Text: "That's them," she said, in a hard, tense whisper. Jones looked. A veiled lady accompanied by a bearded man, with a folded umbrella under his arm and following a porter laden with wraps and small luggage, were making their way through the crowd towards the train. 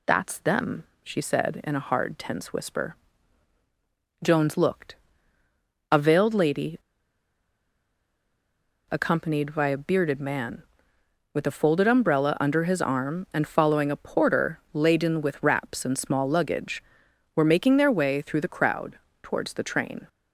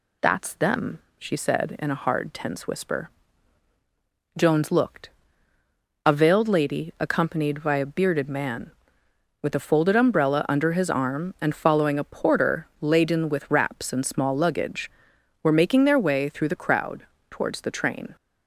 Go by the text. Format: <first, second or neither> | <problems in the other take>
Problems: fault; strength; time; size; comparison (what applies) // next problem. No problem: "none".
second | pauses between "lady" and "accompanied"; strong; at 6.7 s; 2.1 s long // pauses between "crowd" and "towards"; slight; at 18.9 s; 0.24 s long; slight in the second